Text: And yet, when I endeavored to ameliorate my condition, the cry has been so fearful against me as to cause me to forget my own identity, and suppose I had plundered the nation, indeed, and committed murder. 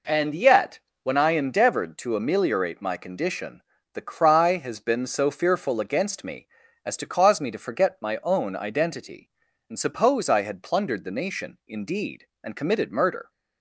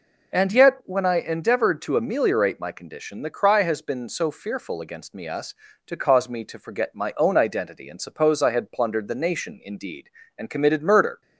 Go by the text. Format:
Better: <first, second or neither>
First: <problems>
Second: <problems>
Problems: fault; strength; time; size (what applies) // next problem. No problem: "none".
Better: first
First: none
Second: says "us" for "as"; at 5.2 s